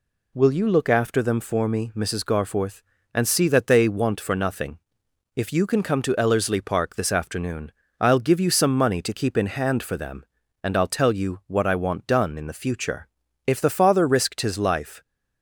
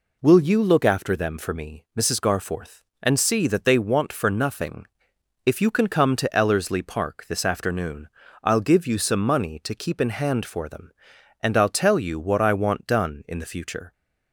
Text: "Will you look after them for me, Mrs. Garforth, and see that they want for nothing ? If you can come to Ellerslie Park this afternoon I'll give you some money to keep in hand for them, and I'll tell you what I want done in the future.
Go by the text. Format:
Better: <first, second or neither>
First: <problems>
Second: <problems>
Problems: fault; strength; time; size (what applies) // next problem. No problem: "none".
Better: second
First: pauses between "afternoon" and "I'll"; slight; at 7.7 s; 0.30 s long // goes on to say "If the father risked his life"; from 13.4 s on; 1.5 s long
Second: pauses between "afternoon" and "I'll"; slight; at 8.0 s; 0.34 s long